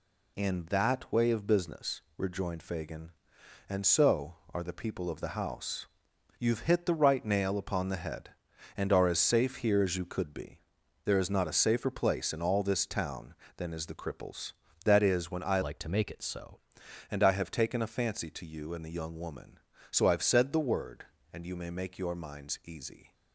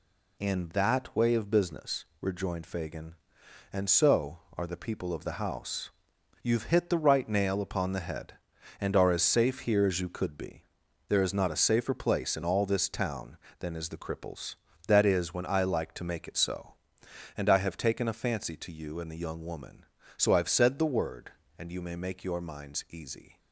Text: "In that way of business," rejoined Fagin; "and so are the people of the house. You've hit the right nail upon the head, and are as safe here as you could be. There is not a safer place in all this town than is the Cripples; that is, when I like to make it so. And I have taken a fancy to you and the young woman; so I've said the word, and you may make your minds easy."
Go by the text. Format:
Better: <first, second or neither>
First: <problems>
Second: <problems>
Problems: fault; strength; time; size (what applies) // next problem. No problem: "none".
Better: second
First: changes voice from "like" to "so"; from 15.6 to 16.5 s; 0.9 s long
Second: none